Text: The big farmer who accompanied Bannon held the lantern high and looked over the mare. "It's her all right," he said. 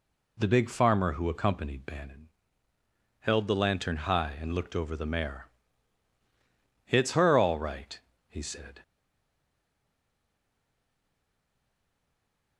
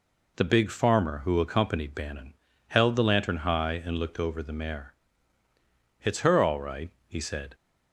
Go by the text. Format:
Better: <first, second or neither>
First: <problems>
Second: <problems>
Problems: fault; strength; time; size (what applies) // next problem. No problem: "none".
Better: second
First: pauses between "Bannon" and "held"; noticeable; at 2.2 s; 0.90 s long // stays silent after the last word; strong; from 8.8 s on; 3.7 s long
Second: pauses between "Bannon" and "held"; slight; at 2.3 s; 0.34 s long